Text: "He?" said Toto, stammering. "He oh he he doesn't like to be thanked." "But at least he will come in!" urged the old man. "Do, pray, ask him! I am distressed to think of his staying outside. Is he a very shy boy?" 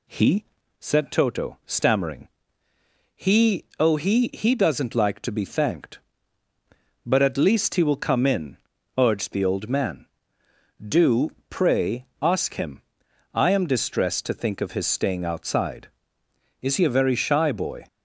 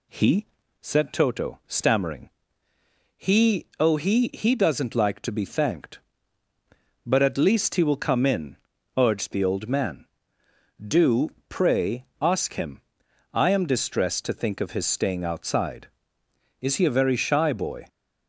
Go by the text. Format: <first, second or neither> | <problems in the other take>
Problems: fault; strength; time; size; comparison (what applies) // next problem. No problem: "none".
neither | none